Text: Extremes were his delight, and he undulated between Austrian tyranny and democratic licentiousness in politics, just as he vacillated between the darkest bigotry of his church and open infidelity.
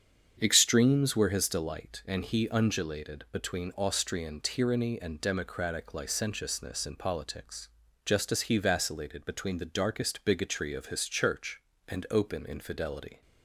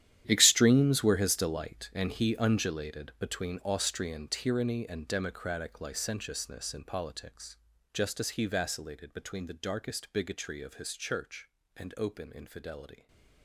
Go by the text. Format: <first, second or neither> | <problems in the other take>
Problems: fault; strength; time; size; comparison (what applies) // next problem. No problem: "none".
first | gets quieter; strong; throughout; 16 dB // starts louder than the rest; strong; until 1.2 s; 11 dB; strong in the first